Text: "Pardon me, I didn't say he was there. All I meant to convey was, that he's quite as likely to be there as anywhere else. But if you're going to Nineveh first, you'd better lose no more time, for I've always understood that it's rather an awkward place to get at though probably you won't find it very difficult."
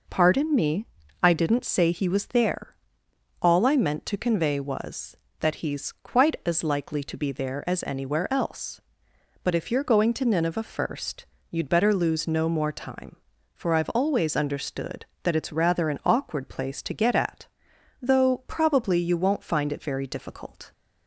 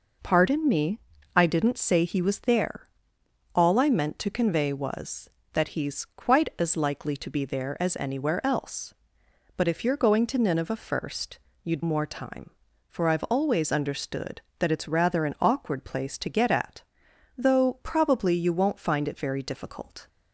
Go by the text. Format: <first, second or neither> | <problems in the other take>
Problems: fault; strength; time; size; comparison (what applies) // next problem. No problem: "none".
first | skips "better lose no"; at 11.8 s // pauses between "at" and "though"; noticeable; at 16.8 s; 0.56 s long; noticeable in the first